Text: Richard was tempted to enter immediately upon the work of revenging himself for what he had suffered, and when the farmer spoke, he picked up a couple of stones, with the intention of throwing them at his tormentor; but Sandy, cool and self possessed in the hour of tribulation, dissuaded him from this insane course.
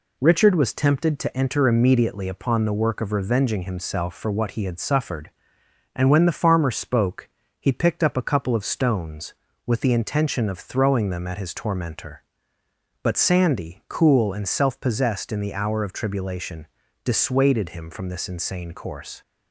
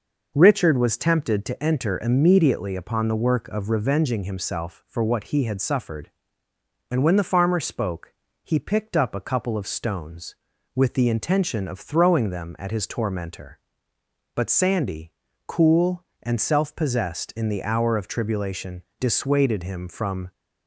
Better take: first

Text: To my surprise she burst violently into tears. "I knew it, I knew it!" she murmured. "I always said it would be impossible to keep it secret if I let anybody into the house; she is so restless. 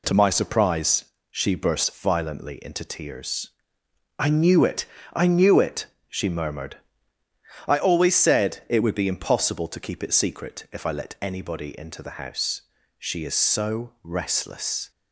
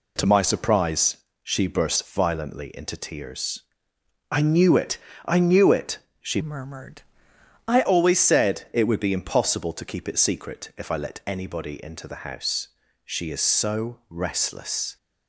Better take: first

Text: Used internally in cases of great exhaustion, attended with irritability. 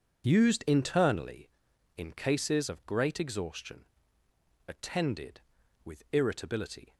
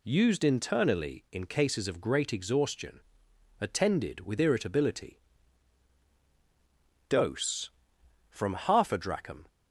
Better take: first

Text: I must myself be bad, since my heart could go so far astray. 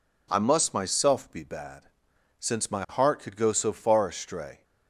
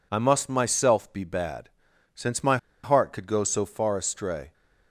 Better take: first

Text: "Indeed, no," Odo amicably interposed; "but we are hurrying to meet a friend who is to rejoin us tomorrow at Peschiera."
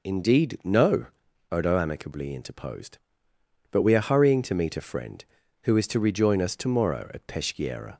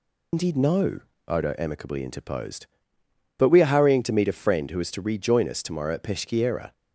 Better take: first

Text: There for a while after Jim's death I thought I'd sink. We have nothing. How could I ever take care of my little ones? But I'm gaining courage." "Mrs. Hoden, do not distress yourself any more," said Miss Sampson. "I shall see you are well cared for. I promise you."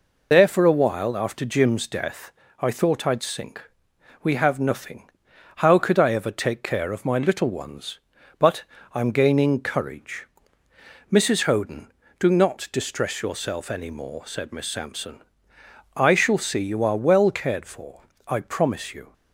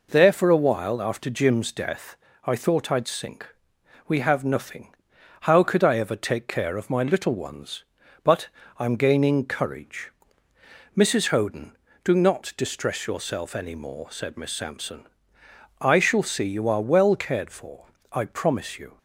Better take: second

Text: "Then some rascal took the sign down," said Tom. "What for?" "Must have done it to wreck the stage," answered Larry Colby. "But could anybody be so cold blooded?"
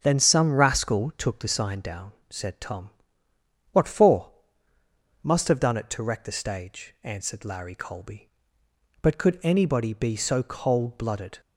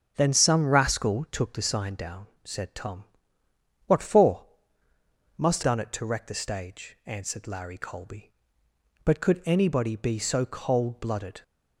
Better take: first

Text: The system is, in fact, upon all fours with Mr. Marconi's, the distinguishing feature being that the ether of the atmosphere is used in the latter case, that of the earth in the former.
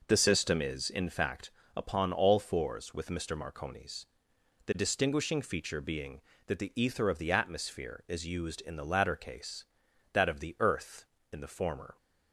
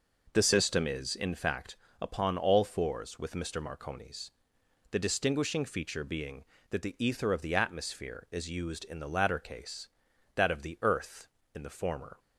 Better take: neither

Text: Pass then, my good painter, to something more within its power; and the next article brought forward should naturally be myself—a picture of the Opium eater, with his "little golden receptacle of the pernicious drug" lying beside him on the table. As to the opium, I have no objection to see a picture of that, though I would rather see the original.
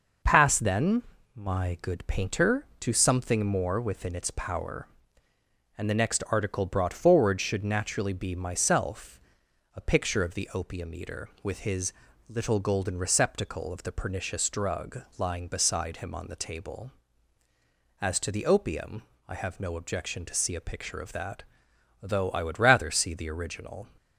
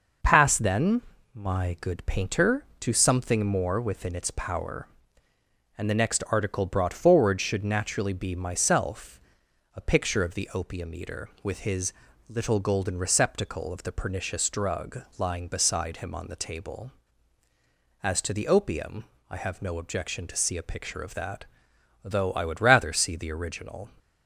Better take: neither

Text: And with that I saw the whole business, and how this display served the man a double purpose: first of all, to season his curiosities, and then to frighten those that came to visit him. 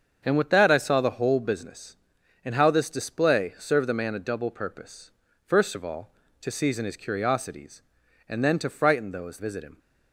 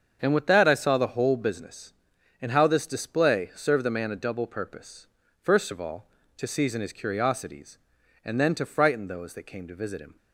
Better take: second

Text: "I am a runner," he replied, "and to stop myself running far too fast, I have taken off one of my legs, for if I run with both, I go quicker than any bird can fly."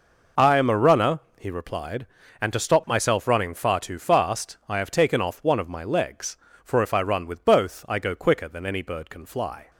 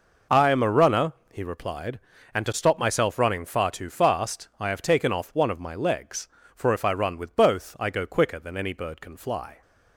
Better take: neither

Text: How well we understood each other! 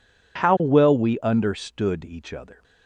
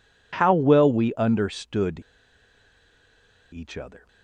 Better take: first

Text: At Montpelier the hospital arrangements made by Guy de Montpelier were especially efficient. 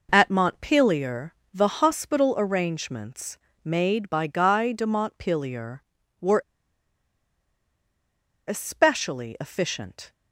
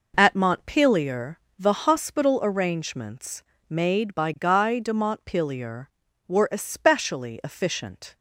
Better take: second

